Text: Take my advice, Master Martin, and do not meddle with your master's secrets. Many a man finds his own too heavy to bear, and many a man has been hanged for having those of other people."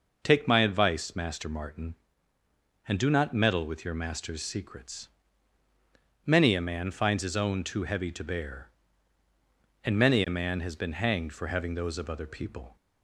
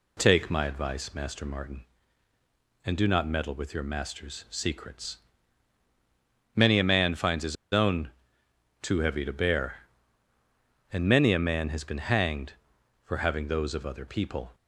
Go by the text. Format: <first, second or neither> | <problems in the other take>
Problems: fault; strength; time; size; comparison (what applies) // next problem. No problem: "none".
first | pauses between "his" and "own"; slight; at 7.5 s; 0.16 s long // pauses between "own" and "too"; noticeable; at 8.0 s; 0.74 s long